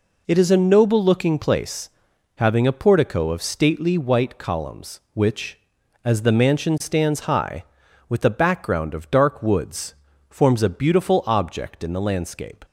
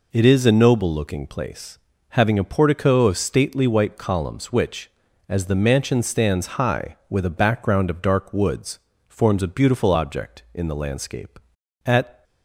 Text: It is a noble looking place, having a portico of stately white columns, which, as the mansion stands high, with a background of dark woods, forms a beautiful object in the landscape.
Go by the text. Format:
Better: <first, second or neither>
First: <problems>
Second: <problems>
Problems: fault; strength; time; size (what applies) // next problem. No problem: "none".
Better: first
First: none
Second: goes on to say "At"; slight; from 11.8 s on; 0.40 s long